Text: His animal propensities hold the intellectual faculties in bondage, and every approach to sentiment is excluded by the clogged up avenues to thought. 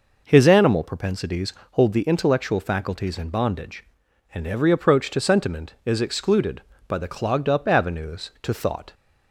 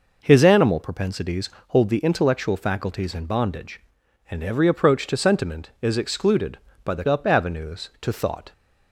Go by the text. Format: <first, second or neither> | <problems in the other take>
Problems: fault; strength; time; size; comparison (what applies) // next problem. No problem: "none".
first | pauses between "propensities" and "hold"; slight; at 1.4 s; 0.20 s long; slight in the first // skips "clogged"; at 7.0 s